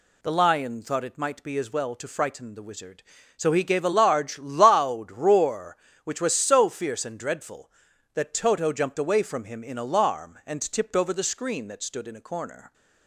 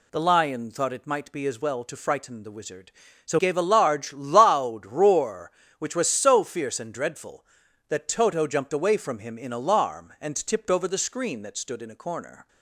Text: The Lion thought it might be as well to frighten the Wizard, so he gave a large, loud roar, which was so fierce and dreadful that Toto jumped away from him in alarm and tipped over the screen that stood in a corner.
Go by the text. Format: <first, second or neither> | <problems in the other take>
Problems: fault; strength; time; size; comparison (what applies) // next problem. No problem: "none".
first | skips "he"; at 3.3 s